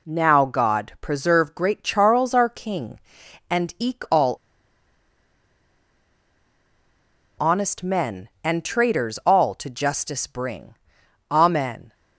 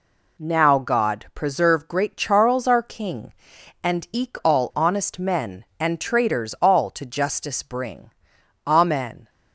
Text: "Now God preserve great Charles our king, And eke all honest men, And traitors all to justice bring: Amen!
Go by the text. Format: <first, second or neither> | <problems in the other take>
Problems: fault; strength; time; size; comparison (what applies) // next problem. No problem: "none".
second | pauses between "all" and "honest"; strong; at 4.3 s; 3.0 s long